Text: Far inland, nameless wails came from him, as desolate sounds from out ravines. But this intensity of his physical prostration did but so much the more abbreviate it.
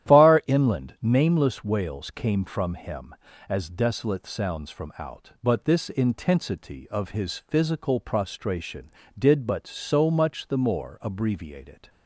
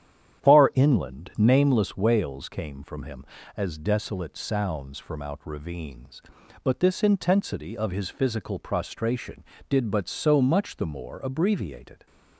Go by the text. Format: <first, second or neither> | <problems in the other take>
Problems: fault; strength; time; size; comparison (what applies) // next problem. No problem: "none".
second | starts louder than the rest; strong; until 1.2 s; 11.5 dB; strong in the second // skips "ravines"; at 5.3 s